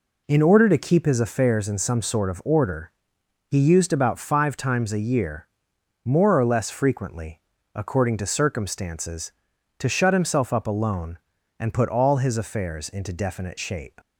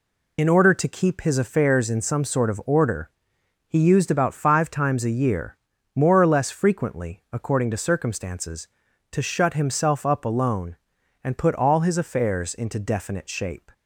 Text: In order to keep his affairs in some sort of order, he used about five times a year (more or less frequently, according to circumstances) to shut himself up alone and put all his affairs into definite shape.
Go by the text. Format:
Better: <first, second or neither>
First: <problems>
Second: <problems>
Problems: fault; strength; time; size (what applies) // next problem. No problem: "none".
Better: first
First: none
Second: loses the start of "In"; at 0.3 s; 55 ms